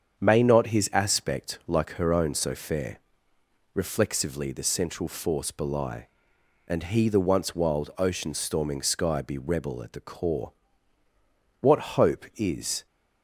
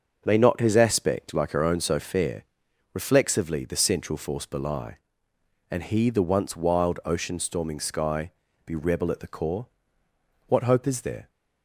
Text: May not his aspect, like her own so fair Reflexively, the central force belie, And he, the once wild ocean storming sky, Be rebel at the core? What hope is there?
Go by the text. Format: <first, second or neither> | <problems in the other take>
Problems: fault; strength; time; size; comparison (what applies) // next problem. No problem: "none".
second | starts louder than the rest; strong; until 1.2 s; 7.5 dB; also in the second // pauses between "fair" and "Reflexively"; noticeable; at 2.9 s; 0.76 s long; noticeable in the second // stops before "there"; at 12.8 s